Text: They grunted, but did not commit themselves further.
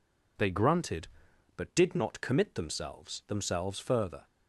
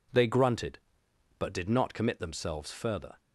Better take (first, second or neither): second